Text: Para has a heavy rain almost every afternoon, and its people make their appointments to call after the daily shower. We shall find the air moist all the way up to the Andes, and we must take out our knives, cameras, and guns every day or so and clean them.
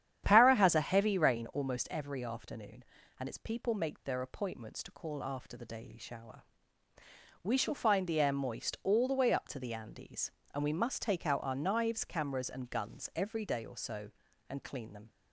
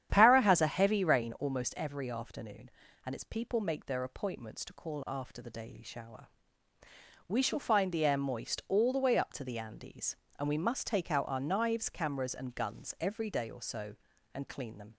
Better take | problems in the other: neither | starts louder than the rest; strong; the same in both

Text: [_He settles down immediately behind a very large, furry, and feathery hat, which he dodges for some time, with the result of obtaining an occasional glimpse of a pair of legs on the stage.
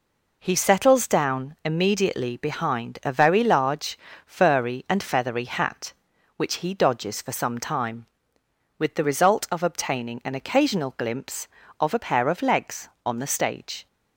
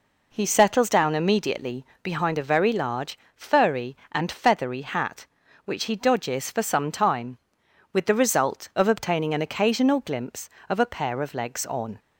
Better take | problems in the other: first | pauses between "immediately" and "behind"; slight; at 1.8 s; 0.20 s long // stops before "the stage"; at 11.9 s

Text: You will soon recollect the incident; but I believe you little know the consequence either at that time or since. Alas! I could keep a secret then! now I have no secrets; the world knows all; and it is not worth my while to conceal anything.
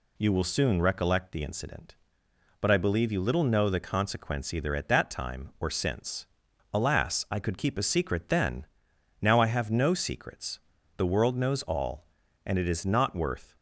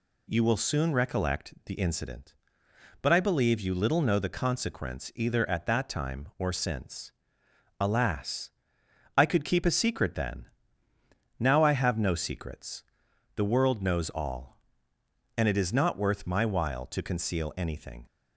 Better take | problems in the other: second | stops before "my while to conceal anything"; at 13.5 s

